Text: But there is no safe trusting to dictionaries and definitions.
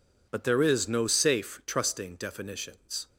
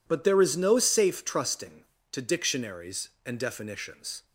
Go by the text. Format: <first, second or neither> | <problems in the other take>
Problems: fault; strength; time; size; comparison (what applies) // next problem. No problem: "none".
second | skips "to dictionaries and"; at 2.1 s